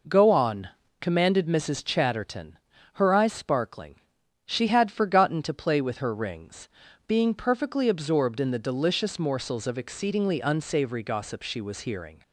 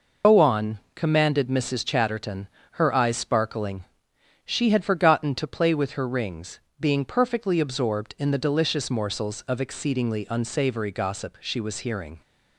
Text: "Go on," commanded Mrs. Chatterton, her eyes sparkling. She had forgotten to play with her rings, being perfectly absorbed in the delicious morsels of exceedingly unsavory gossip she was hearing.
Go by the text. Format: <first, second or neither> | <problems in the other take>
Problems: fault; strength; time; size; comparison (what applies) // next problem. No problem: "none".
first | loses the start of "Go"; at 0.2 s; 150 ms